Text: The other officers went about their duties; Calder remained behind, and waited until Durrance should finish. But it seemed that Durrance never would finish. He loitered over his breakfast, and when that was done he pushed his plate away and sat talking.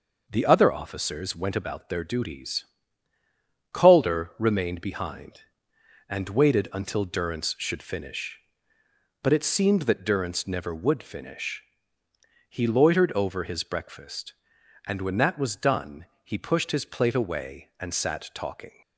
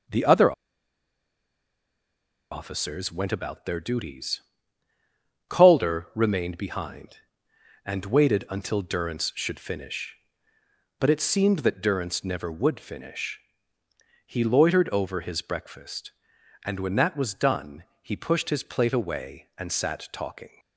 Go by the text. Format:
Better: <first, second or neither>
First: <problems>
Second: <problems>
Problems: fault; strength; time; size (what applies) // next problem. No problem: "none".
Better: first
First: pauses between "done" and "he"; slight; at 16.0 s; 0.16 s long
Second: pauses between "other" and "officers"; strong; at 0.5 s; 1.9 s long // pauses between "done" and "he"; slight; at 17.8 s; 0.16 s long